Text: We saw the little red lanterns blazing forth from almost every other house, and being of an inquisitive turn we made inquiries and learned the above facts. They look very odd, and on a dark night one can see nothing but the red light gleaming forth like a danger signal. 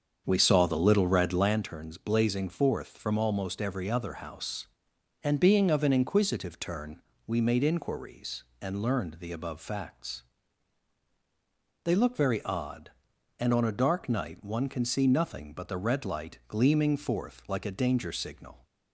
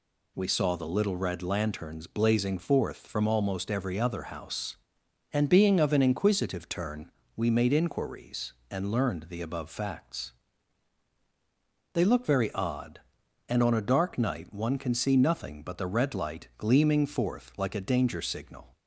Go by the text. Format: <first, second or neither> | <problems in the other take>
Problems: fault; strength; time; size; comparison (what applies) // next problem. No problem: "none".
second | starts louder than the rest; until 1.6 s; 7 dB // pauses between "turn" and "we"; slight; at 7.0 s; 0.26 s long; slight in the second